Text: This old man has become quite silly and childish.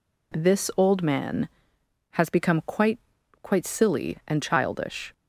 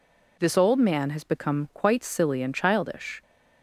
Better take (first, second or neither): second